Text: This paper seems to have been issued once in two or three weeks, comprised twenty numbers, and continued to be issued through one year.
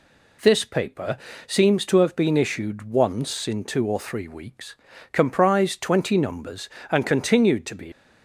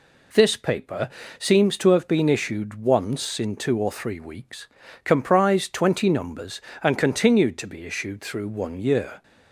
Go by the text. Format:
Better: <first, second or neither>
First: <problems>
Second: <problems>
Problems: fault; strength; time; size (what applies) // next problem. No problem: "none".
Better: second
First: pauses between "paper" and "seems"; slight; at 1.1 s; 0.30 s long // stops before "issued through one year"; at 7.9 s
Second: pauses between "paper" and "seems"; slight; at 1.0 s; 0.30 s long